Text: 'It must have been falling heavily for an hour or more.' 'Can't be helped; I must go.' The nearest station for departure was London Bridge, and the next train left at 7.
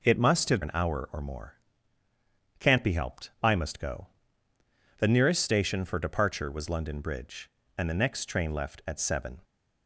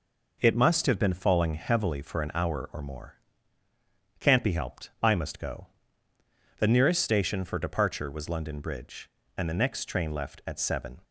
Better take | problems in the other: second | skips "been falling heavily for"; at 0.6 s

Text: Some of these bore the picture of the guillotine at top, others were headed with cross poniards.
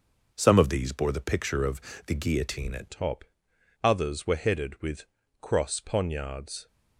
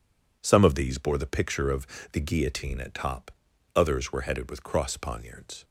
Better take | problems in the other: second | pauses between "of" and "the"; slight; at 1.7 s; 0.28 s long; slight in the second // changes voice at "top"; from 2.9 s on; 3.7 s long // pauses between "with" and "cross"; slight; at 5.0 s; 0.36 s long

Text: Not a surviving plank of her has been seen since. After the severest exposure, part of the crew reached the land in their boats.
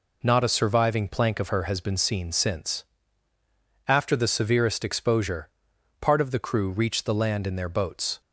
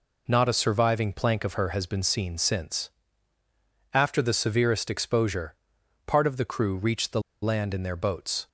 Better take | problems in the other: first | pauses between "the" and "land"; slight; at 7.2 s; 0.20 s long

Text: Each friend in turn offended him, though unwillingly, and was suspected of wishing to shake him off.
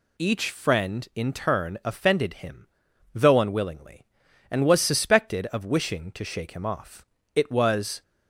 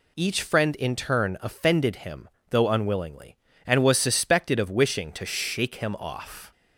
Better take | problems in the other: second | goes on to say "It was"; noticeable; from 7.3 s on; 0.68 s long

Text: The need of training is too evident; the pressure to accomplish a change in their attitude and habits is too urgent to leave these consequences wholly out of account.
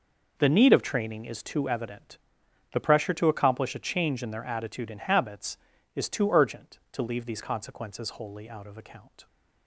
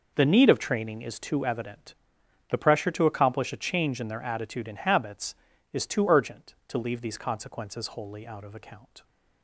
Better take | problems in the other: neither | none

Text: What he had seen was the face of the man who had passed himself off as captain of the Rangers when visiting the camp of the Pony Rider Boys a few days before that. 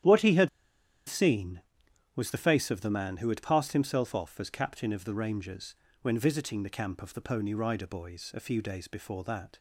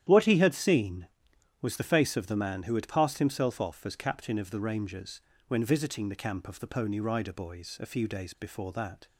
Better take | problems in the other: second | starts louder than the rest; strong; until 2.1 s; 10.5 dB; strong in the second // pauses between "had" and "seen"; noticeable; at 0.4 s; 0.58 s long // pauses between "Rangers" and "when"; slight; at 5.7 s; 0.30 s long; slight in the second

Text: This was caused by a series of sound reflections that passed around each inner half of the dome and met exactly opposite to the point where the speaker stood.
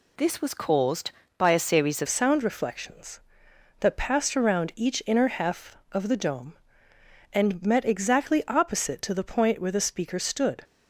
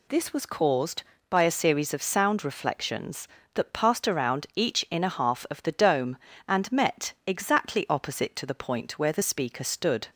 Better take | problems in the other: second | changes voice at "sound"; from 2.0 s on; 8.6 s long

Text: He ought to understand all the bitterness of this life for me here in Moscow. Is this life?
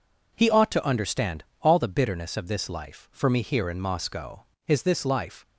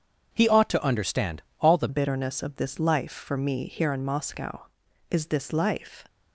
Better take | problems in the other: first | starts louder than the rest; strong; until 1.3 s; 7.5 dB // pauses between "understand" and "all"; slight; at 1.4 s; 0.18 s long; slight in the first // changes voice at "bitterness"; from 1.8 s on; 4.2 s long

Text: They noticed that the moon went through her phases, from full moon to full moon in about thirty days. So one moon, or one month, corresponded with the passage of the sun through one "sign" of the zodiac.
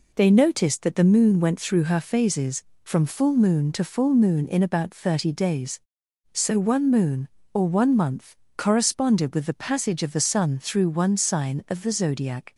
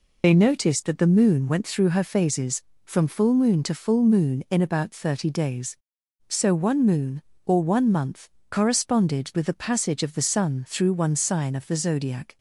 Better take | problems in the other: first | loses the start of "They"; at 0.2 s; 45 ms

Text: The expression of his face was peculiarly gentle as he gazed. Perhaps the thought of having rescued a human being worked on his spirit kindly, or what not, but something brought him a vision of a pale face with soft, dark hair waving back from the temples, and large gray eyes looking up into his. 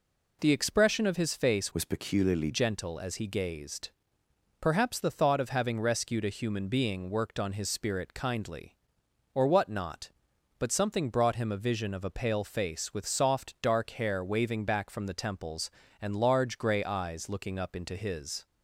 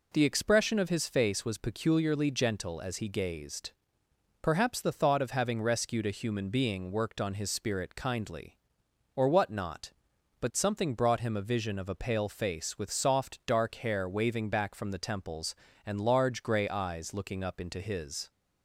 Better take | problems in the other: second | changes voice from "was" to "peculiarly"; from 1.7 to 2.4 s; 0.7 s long

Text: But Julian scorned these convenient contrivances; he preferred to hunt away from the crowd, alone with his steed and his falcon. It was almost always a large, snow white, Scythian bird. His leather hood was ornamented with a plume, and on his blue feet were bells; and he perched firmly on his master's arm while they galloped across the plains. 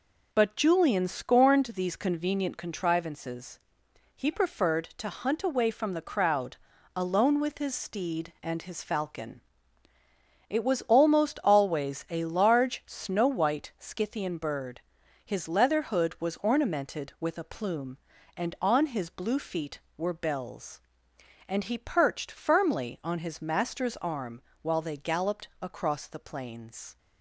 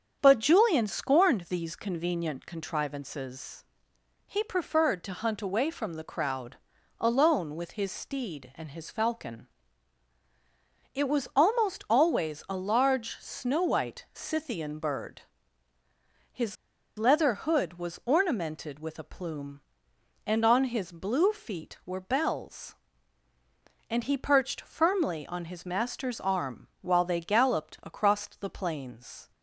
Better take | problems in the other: first | starts louder than the rest; strong; until 1.2 s; 7.5 dB // pauses between "His" and "leather"; at 16.5 s; 0.43 s long // pauses between "arm" and "while"; slight; at 26.6 s; 0.16 s long; slight in the first

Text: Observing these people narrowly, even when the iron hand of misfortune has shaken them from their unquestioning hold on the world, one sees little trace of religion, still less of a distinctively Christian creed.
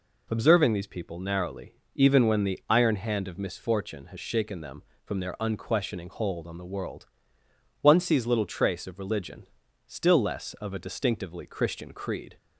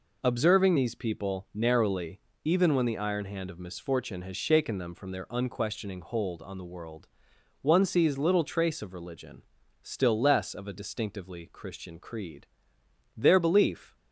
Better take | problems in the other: first | goes on to say "Their belief"; noticeable; from 13.1 s on; 0.80 s long

